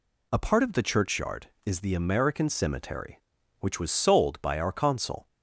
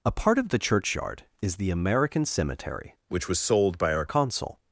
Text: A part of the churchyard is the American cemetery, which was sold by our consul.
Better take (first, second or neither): first